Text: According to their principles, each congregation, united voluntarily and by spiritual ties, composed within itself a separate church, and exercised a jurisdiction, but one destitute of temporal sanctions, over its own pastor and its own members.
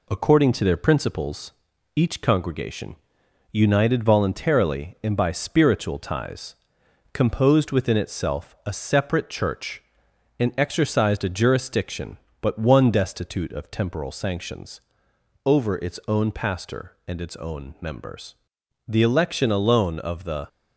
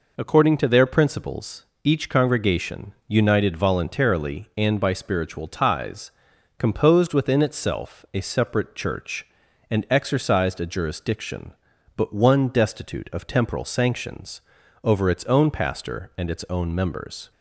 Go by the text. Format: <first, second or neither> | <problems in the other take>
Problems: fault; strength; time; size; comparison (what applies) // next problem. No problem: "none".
second | goes on to say "The election alone of the"; from 18.8 s on; 1.6 s long